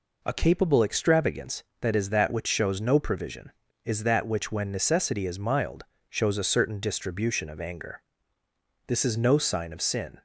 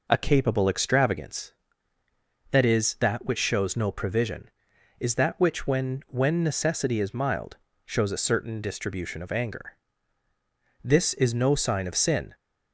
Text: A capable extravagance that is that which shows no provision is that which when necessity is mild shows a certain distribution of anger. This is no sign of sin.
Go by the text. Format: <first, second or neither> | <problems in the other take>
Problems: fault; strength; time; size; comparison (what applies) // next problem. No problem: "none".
first | says "when" twice; at 6.0 s // pauses between "mild" and "shows"; slight; at 7.5 s; 0.30 s long; slight in the first